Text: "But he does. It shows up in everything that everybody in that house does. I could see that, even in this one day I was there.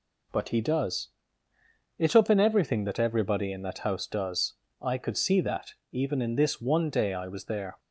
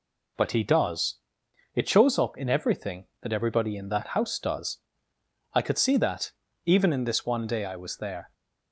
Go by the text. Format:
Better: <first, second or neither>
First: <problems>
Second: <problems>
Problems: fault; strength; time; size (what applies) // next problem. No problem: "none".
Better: second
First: skips "shows"; at 2.1 s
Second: none